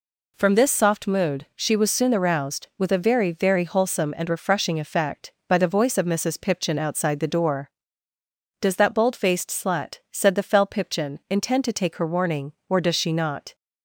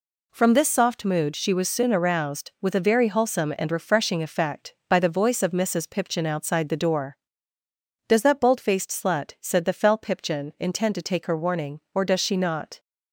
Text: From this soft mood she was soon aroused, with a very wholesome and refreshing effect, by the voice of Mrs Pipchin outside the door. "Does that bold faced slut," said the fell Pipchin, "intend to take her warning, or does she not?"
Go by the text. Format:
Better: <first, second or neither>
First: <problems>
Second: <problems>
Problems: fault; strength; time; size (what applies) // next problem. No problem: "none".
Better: second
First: says "very" twice; at 3.3 s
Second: none